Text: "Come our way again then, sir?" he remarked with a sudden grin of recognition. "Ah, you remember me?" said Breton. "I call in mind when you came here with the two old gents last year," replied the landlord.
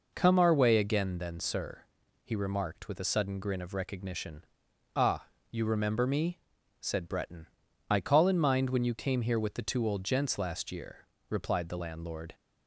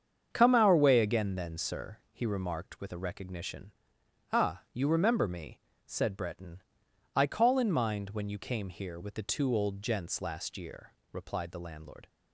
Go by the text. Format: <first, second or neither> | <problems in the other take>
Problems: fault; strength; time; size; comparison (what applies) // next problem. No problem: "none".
first | starts louder than the rest; strong; until 1.3 s; 7.5 dB // skips "sudden grin of"; at 2.9 s